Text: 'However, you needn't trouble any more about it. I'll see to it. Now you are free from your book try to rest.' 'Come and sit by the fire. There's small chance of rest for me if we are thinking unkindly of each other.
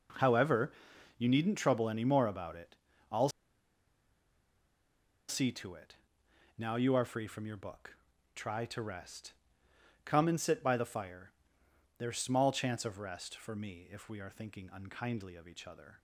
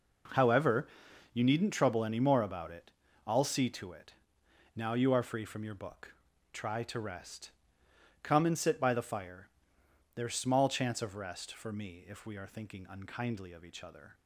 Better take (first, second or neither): second